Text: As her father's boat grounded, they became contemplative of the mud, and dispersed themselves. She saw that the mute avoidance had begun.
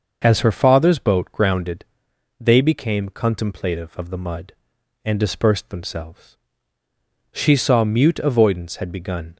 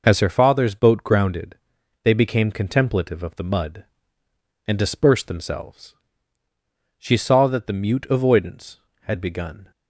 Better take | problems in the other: second | starts louder than the rest; until 1.2 s; 6 dB // skips "that the"; at 7.8 s

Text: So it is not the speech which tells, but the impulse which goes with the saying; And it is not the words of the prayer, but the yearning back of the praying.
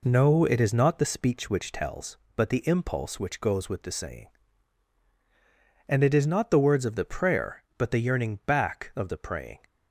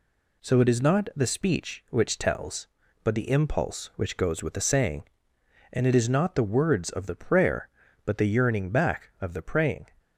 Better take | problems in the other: second | says "No" for "So"; at 0.0 s

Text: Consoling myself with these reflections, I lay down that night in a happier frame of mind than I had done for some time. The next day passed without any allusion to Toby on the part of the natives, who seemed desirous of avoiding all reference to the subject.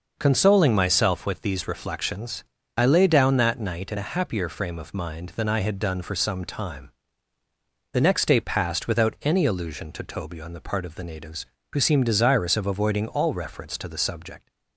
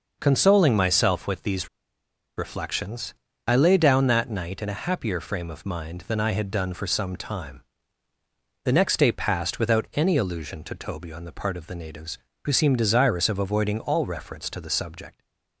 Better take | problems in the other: first | pauses between "these" and "reflections"; noticeable; at 1.6 s; 0.69 s long

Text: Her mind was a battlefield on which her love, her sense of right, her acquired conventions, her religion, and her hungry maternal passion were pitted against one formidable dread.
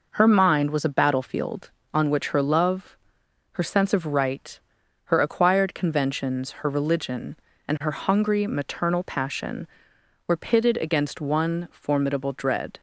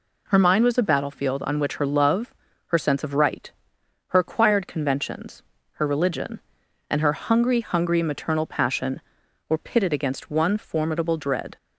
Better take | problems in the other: first | says "hungry" twice; at 7.5 s

